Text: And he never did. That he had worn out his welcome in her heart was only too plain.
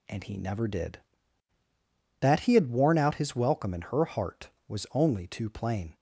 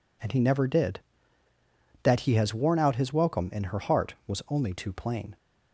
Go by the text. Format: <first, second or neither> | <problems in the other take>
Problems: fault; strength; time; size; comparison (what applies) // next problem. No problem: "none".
first | says "has" for "had"; at 2.3 s